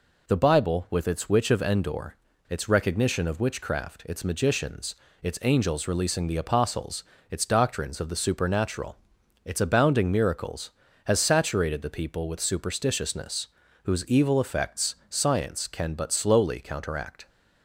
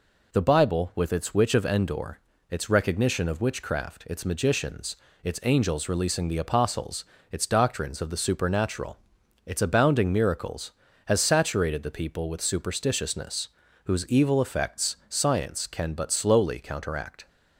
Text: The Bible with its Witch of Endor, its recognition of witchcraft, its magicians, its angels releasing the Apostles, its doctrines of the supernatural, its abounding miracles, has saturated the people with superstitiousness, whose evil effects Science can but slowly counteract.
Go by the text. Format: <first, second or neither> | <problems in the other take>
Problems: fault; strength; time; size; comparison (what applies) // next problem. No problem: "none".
neither | none